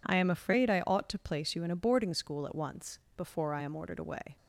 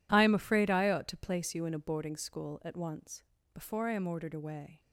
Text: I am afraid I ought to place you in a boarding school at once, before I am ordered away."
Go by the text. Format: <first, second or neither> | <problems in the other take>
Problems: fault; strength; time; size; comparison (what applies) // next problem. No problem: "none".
neither | none